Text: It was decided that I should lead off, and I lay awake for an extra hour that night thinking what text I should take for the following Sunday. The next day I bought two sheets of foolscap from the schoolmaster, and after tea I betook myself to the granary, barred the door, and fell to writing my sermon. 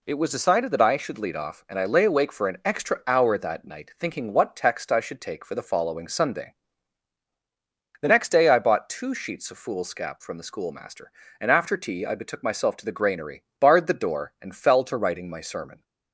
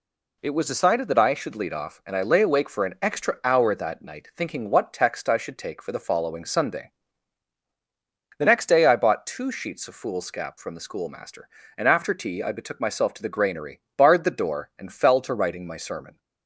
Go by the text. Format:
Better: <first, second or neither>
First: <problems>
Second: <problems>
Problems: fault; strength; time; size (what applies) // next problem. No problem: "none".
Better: neither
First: none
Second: none